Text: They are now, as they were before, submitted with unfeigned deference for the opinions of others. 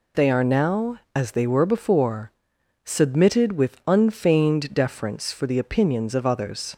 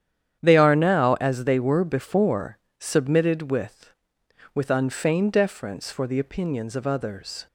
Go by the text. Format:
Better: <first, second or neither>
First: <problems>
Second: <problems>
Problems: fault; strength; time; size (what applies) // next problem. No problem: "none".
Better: first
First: none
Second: starts louder than the rest; strong; until 1.4 s; 9.5 dB // says "with" twice; at 4.5 s